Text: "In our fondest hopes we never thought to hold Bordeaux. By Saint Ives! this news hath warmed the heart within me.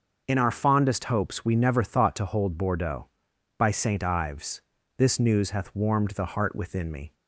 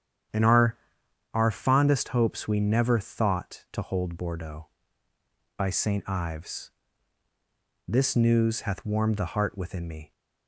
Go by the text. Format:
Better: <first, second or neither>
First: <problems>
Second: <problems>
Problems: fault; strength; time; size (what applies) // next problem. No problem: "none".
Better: first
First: starts louder than the rest; until 1.2 s; 6.5 dB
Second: starts louder than the rest; strong; until 1.8 s; 9 dB // says "our" twice; at 1.3 s